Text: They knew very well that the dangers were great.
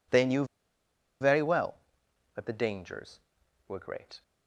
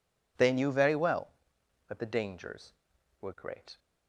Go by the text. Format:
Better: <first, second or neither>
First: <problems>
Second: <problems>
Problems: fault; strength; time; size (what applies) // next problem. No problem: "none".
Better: second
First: pauses between "knew" and "very"; noticeable; at 0.4 s; 0.76 s long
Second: none